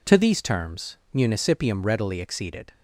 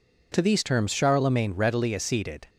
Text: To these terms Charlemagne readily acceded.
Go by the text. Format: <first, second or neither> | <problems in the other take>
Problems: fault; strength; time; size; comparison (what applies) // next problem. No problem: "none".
second | says "Municipium" for "Charlemagne"; at 1.1 s